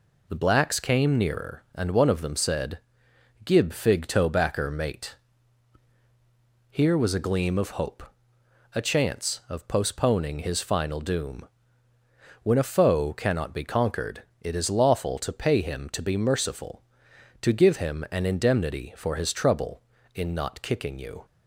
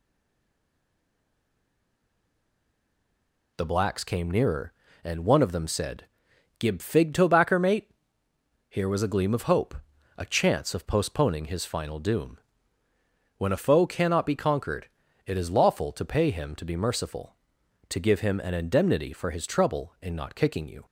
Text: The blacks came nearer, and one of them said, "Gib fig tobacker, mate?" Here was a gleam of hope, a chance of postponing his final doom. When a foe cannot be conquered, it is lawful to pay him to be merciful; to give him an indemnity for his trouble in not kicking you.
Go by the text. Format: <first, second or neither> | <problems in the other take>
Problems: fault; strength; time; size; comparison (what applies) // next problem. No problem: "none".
first | stays silent before the first word; strong; until 3.5 s; 3.5 s long